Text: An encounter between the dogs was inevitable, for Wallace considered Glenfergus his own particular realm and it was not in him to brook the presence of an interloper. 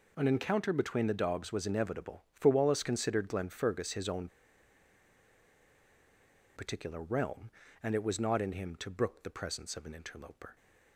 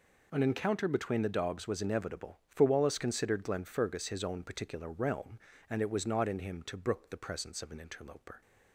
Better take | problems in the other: second | pauses between "own" and "particular"; strong; at 4.2 s; 2.2 s long

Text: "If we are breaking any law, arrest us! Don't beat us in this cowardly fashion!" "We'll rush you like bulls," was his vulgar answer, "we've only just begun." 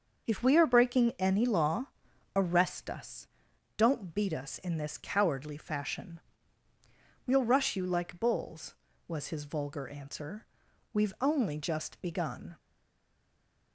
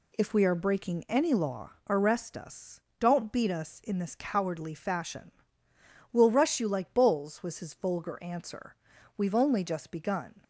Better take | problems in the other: second | stays silent after the last word; from 12.5 s on; 1.2 s long

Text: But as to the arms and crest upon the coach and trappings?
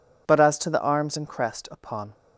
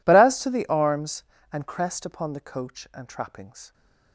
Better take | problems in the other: second | stops before "the coach and trappings"; at 2.1 s

